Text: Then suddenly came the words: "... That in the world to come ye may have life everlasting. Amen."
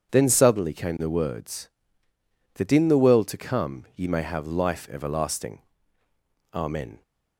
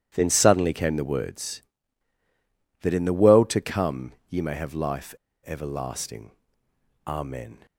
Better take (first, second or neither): first